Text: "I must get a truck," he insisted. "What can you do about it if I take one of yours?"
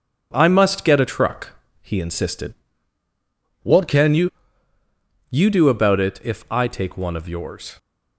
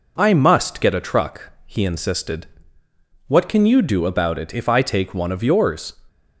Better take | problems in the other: second | says "you" twice; at 5.2 s

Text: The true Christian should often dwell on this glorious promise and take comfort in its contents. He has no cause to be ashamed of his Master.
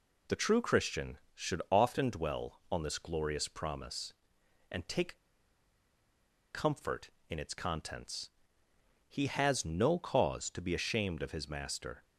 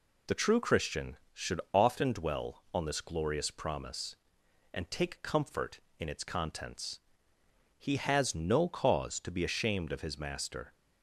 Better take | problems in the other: second | pauses between "take" and "comfort"; strong; at 5.1 s; 1.3 s long

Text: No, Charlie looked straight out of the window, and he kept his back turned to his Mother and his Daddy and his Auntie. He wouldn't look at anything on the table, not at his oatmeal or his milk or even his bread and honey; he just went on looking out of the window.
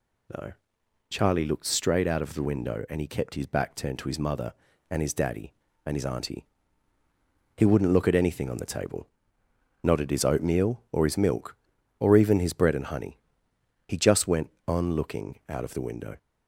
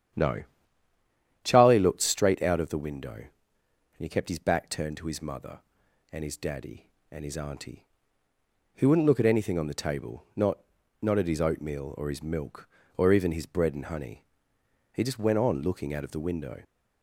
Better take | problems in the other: first | starts louder than the rest; strong; until 2.1 s; 9 dB // says "not" twice; at 11.0 s

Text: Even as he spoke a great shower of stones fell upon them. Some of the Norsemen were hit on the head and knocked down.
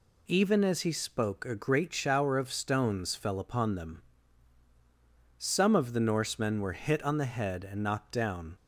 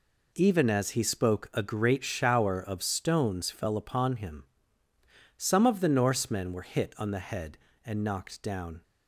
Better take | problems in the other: first | says "him" for "them"; at 4.1 s

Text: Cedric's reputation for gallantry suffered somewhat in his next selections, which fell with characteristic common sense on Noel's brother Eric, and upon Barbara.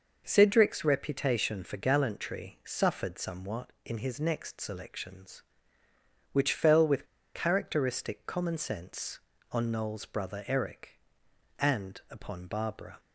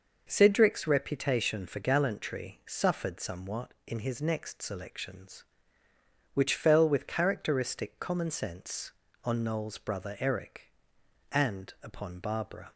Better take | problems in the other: second | pauses between "with" and "characteristic"; slight; at 7.0 s; 0.29 s long

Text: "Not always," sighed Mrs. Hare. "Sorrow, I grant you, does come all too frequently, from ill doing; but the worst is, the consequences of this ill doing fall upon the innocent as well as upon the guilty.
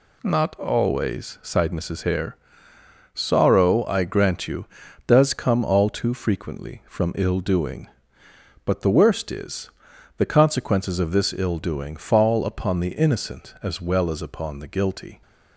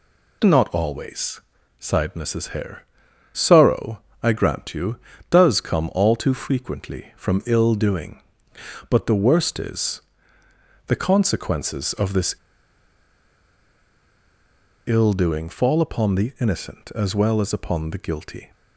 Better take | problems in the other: first | pauses between "this" and "ill"; strong; at 12.3 s; 2.5 s long

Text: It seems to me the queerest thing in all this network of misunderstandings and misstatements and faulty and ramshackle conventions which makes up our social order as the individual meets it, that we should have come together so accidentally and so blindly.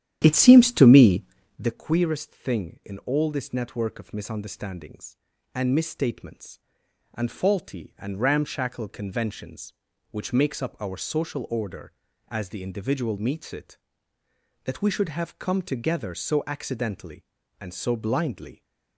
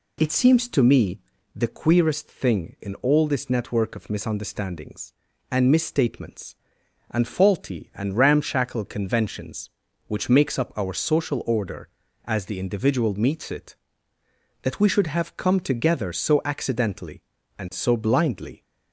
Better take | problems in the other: second | starts louder than the rest; strong; until 1.8 s; 11 dB // pauses between "me" and "the"; slight; at 1.2 s; 0.36 s long; slight in the second

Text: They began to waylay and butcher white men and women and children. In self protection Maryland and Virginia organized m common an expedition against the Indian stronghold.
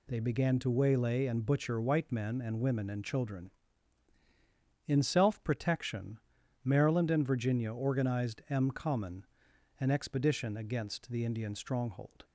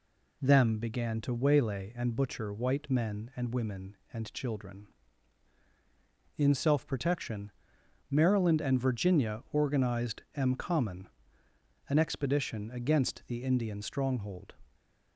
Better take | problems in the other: first | says "Them" for "They"; at 0.4 s // pauses between "protection" and "Maryland"; noticeable; at 7.5 s; 0.60 s long; noticeable in the first // pauses between "common" and "an"; noticeable; at 11.0 s; 0.82 s long; noticeable in the first // stays silent after the last word; slight; from 14.6 s on; 0.5 s long

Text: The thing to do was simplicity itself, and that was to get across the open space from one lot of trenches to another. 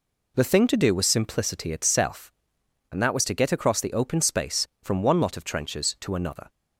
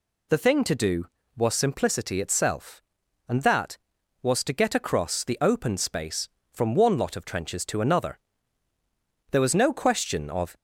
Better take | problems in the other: first | goes on to say "There was no question of"; noticeable; from 9.3 s on; 1.2 s long

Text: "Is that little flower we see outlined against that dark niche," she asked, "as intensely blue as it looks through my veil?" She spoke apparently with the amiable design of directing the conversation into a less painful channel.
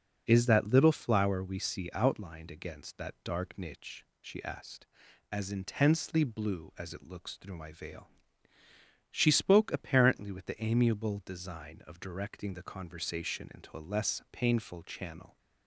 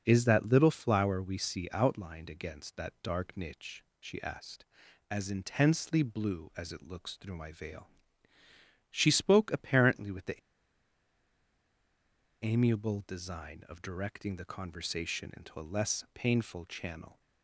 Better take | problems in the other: first | pauses between "the" and "amiable"; strong; at 10.3 s; 2.0 s long

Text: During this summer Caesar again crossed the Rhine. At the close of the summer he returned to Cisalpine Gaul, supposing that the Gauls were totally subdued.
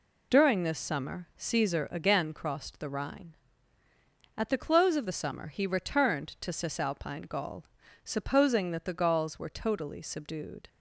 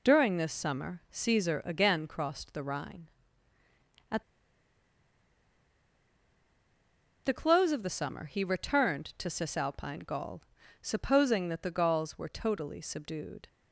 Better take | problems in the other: first | pauses between "At" and "the"; strong; at 4.2 s; 3.0 s long

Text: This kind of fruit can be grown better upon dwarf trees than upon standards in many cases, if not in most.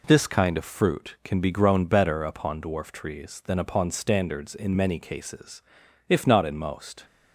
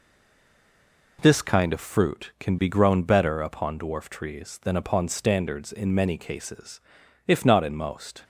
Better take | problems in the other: first | stays silent before the first word; noticeable; until 1.1 s; 1.1 s long

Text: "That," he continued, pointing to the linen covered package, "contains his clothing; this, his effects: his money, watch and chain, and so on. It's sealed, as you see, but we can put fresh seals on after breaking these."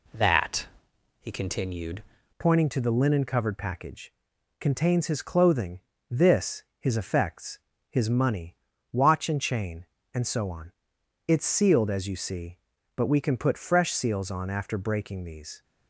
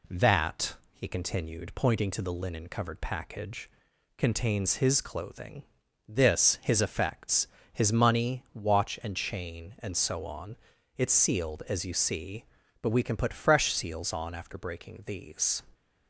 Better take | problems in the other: second | changes voice at "pointing"; from 2.3 s on; 13.3 s long

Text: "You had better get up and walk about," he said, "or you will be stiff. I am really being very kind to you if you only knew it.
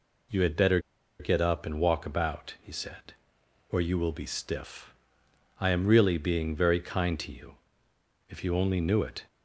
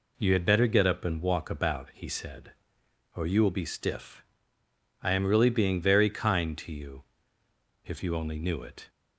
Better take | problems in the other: second | pauses between "better" and "get"; at 0.7 s; 0.41 s long // pauses between "you" and "if"; noticeable; at 7.5 s; 0.74 s long; noticeable in the second

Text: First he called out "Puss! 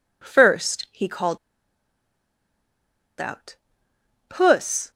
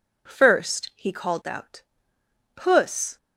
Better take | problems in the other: second | pauses between "called" and "out"; strong; at 1.3 s; 1.8 s long // pauses between "out" and "Puss"; noticeable; at 3.5 s; 0.74 s long; noticeable in the second

